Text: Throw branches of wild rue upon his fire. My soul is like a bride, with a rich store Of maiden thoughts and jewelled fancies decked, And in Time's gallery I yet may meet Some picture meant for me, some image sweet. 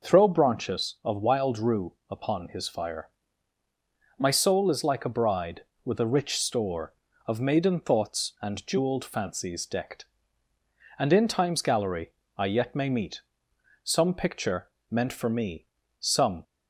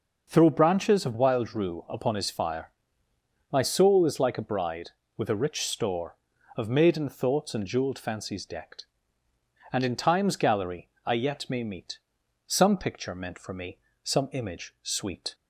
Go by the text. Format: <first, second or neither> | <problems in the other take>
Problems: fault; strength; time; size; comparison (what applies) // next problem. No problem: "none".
second | pauses between "rue" and "upon"; slight; at 1.9 s; 0.18 s long // pauses between "gallery" and "I"; slight; at 12.1 s; 0.26 s long; slight in the second // pauses between "meet" and "Some"; noticeable; at 13.2 s; 0.64 s long; noticeable in the second // pauses between "picture" and "meant"; slight; at 14.6 s; 0.24 s long // stops before "image sweet"; at 16.4 s